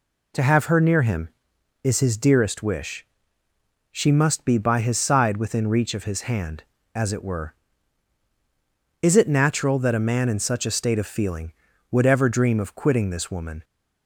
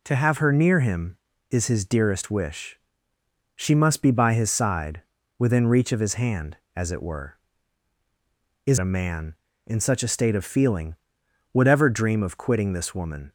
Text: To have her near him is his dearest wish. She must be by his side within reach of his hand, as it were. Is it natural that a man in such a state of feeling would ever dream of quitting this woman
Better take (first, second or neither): first